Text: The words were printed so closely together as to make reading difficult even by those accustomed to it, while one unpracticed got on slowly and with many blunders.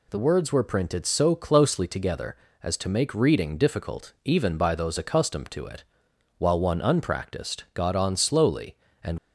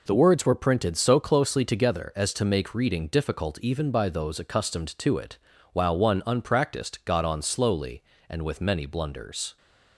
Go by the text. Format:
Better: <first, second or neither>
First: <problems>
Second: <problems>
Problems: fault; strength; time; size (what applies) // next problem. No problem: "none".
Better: second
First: stops before "with many blunders"; at 9.1 s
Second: none